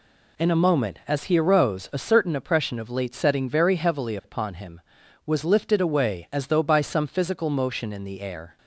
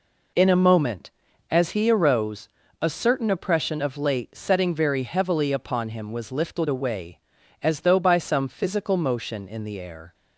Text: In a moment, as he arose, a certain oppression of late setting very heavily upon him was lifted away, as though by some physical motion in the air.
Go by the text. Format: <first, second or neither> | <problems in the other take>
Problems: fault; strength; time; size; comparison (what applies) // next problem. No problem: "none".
neither | none